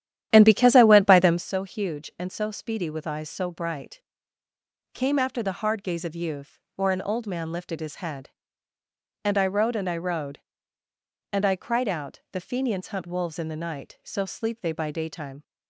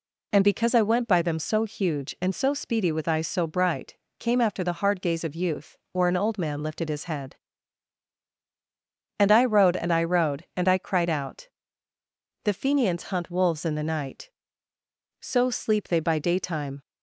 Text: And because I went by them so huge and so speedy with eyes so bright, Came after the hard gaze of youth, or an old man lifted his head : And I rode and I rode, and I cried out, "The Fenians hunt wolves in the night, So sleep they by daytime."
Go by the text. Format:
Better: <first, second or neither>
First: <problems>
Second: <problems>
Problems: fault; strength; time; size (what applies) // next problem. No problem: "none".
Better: second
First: starts louder than the rest; strong; until 1.5 s; 11.5 dB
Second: none